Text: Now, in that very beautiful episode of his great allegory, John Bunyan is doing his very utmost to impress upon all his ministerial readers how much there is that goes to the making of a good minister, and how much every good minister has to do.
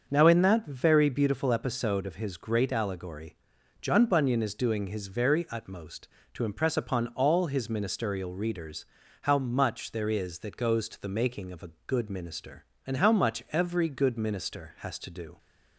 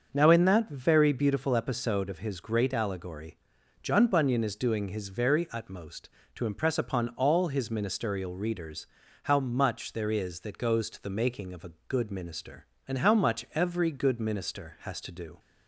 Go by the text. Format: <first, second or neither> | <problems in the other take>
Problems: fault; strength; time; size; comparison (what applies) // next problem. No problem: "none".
neither | starts louder than the rest; the same in both // pauses between "readers" and "how"; the same in both // pauses between "a" and "good"; slight; the same in both